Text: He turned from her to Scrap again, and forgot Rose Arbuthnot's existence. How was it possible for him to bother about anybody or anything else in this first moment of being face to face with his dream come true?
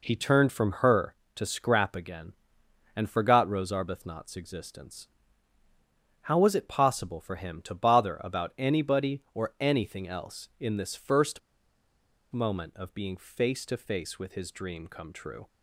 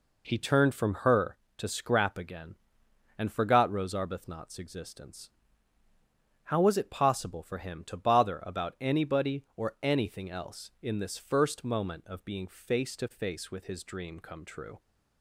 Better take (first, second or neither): second